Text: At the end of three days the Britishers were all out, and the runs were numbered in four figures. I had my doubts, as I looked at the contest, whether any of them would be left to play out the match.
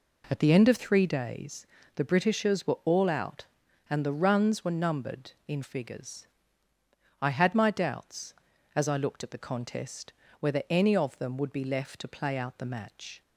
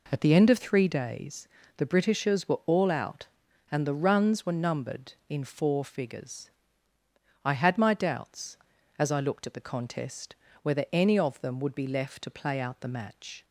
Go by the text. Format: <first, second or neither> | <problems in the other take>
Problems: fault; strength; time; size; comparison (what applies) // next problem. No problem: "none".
second | pauses between "days" and "the"; slight; at 1.6 s; 0.28 s long; slight in the second // skips "four"; at 5.6 s